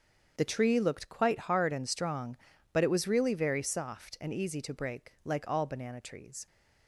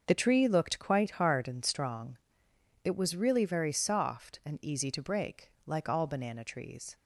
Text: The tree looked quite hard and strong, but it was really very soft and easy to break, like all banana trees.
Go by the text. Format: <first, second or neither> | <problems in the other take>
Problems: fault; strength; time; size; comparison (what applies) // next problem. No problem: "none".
first | starts louder than the rest; until 1.0 s; 6 dB; strong in the first // skips "but"; at 2.5 s